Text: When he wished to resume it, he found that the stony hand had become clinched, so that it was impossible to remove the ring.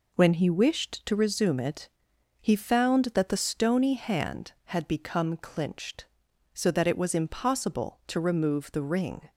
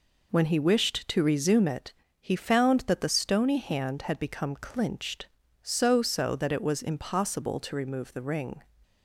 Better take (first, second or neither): first